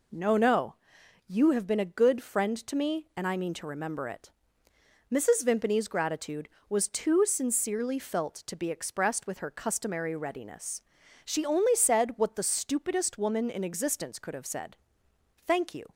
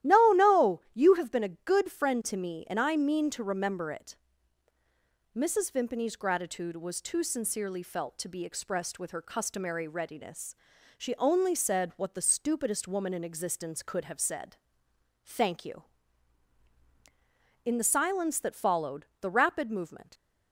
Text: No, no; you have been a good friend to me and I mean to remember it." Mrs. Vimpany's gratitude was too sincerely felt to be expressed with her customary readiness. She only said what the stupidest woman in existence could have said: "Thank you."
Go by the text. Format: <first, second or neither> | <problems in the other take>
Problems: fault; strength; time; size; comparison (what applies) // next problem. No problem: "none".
first | starts louder than the rest; strong; until 1.1 s; 13.5 dB // goes on to say "In the silence that followed the rapid movement"; strong; from 17.6 s on; 2.4 s long